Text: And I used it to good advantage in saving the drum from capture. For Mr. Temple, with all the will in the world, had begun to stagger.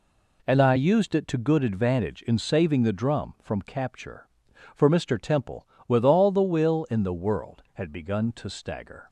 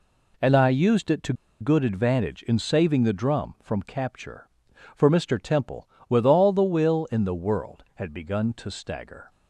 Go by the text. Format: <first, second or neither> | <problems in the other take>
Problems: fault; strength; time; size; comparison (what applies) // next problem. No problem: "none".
first | pauses between "to" and "good"; slight; at 1.3 s; 0.27 s long